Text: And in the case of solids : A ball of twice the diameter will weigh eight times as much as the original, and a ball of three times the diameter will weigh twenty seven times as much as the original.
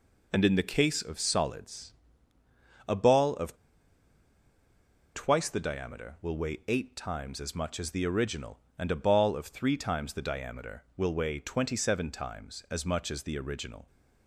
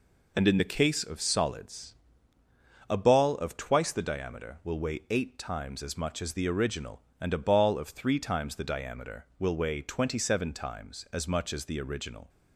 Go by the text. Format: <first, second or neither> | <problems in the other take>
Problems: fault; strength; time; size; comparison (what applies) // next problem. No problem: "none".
second | pauses between "of" and "twice"; strong; at 3.5 s; 1.6 s long